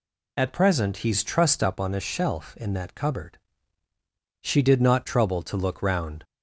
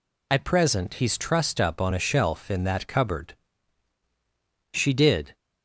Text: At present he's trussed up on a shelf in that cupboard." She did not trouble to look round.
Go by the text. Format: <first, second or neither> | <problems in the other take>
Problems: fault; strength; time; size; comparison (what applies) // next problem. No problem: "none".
first | stops before "not trouble to look round"; at 5.3 s